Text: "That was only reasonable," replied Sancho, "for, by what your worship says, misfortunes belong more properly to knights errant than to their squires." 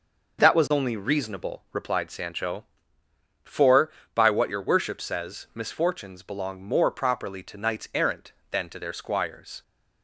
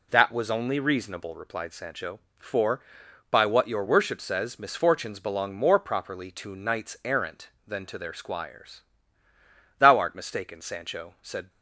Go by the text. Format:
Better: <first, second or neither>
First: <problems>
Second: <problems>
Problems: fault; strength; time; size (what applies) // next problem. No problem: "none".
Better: first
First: none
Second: goes on to say "Thou art mistaken Sancho said"; strong; from 9.7 s on; 1.7 s long